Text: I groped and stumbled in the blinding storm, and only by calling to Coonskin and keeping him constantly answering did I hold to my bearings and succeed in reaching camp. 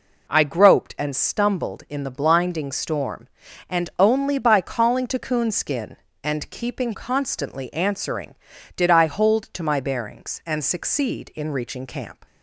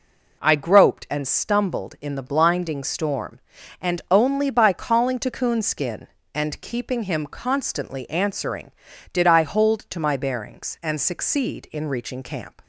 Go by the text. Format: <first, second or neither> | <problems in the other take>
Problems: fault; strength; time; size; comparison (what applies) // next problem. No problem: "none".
second | skips "him"; at 6.9 s